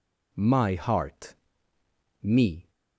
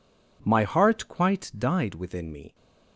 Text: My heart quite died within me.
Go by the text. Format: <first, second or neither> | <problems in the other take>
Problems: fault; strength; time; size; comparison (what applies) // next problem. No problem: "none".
second | skips "quite died within"; at 1.7 s